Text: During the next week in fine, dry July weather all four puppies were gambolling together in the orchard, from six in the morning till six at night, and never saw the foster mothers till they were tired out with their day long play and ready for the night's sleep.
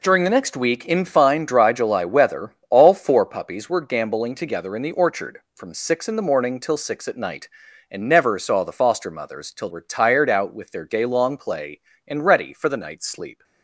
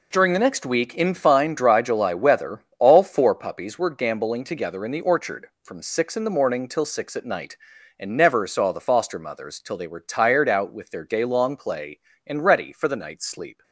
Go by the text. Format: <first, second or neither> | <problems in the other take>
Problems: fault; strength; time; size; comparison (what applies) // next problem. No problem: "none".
second | pauses between "weather" and "all"; slight; at 2.5 s; 0.16 s long; slight in the second // skips "they"; at 9.6 s